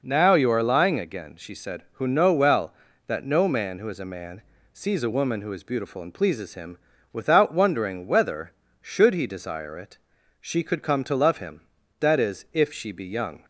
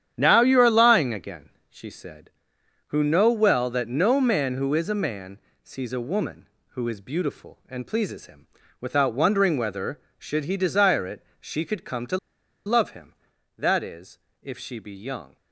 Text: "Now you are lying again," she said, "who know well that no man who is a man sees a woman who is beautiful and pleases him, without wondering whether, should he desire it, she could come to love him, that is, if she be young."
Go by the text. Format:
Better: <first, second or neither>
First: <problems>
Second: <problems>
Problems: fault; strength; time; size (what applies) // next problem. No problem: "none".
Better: first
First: pauses between "man" and "sees"; slight; at 4.4 s; 0.30 s long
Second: starts louder than the rest; strong; until 1.1 s; 9.5 dB // pauses between "man" and "sees"; slight; at 5.3 s; 0.24 s long // pauses between "to" and "love"; noticeable; at 12.1 s; 0.49 s long